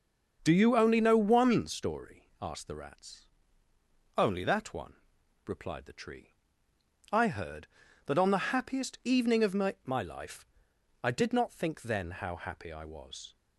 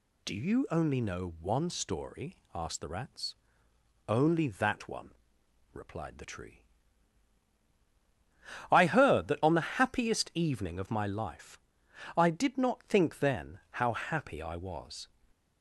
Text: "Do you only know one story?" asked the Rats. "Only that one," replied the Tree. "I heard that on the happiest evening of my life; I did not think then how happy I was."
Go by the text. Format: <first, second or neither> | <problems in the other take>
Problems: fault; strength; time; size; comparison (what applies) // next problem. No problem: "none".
second | starts louder than the rest; until 1.4 s; 6.5 dB // says "my" twice; at 9.8 s